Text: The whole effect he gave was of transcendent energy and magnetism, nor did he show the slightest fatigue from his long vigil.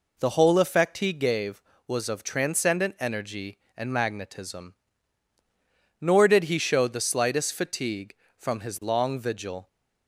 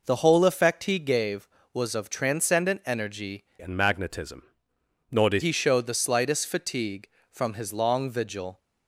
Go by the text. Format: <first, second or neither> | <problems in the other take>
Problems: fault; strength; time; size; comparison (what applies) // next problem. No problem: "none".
first | changes voice from "and" to "did"; from 3.5 to 5.4 s; 1.9 s long